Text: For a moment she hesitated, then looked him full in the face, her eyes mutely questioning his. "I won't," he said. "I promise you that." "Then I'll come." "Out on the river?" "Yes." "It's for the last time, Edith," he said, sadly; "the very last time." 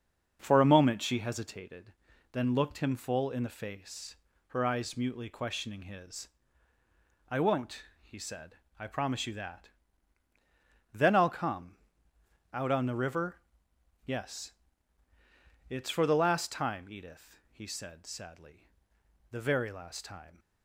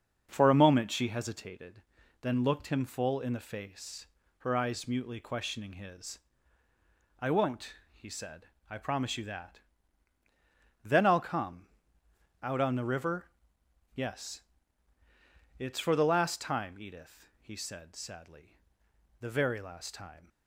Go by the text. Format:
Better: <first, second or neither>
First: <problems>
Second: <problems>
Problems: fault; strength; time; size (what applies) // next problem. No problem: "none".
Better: neither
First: starts louder than the rest; until 1.4 s; 6.5 dB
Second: starts louder than the rest; until 1.3 s; 6.5 dB